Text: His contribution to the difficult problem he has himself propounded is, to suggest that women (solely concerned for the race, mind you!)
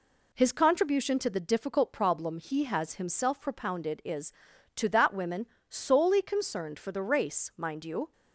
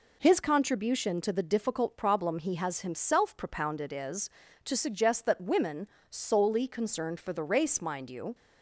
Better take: second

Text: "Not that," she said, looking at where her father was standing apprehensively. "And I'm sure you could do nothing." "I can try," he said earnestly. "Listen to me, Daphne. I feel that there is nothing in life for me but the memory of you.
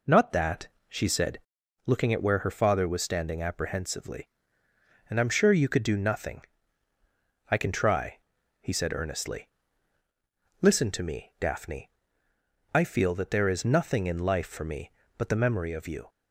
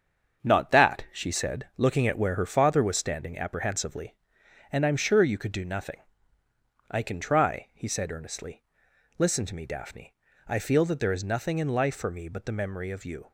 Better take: first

